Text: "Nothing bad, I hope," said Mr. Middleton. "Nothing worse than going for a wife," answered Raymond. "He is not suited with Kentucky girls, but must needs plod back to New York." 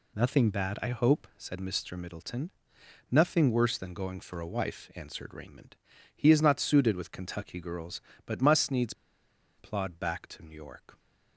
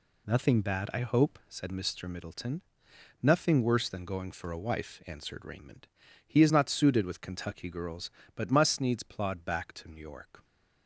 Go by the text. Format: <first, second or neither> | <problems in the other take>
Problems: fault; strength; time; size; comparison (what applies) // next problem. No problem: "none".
second | pauses between "needs" and "plod"; noticeable; at 8.9 s; 0.64 s long